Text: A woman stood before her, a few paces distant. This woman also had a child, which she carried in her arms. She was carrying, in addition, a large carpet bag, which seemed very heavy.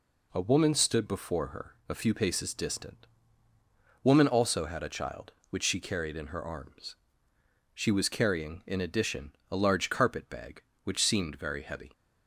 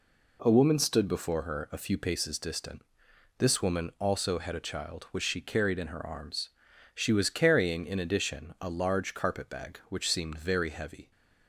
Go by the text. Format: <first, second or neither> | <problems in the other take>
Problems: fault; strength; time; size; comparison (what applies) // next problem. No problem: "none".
second | skips "This"; at 3.5 s